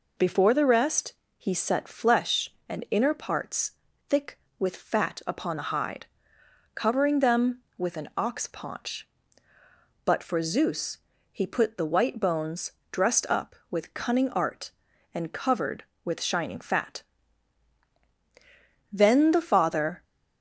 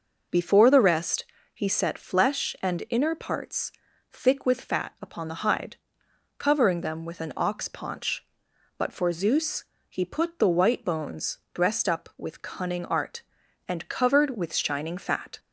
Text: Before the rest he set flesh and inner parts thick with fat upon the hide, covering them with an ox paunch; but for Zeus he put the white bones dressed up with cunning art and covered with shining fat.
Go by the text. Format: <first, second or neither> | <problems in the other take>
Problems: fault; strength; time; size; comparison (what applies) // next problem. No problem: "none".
second | pauses between "rest" and "he"; slight; at 1.1 s; 0.24 s long; slight in the second // pauses between "parts" and "thick"; slight; at 3.7 s; 0.36 s long; also in the second // pauses between "Zeus" and "he"; slight; at 10.9 s; 0.34 s long; slight in the second // pauses between "bones" and "dressed"; slight; at 12.7 s; 0.22 s long // goes on to say "Then the father"; noticeable; from 18.9 s on; 1.1 s long